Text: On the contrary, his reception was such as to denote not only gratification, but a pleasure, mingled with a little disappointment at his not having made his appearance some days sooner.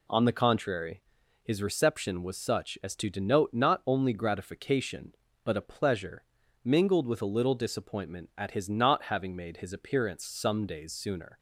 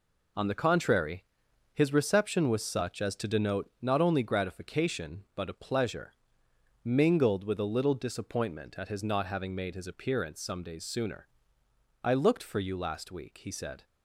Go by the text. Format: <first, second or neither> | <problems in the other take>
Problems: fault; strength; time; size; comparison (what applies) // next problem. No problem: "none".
first | goes on to say "I looked for you last week he said"; strong; from 12.0 s on; 1.8 s long